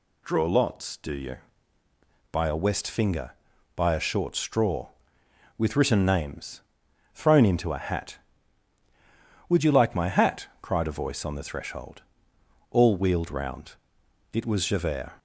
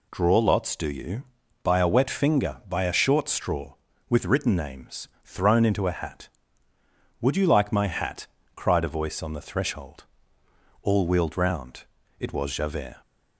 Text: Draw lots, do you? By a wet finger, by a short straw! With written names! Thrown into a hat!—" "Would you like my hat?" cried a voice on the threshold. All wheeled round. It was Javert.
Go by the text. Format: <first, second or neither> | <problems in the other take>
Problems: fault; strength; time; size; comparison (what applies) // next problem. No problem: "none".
second | says "west" for "wet"; at 2.5 s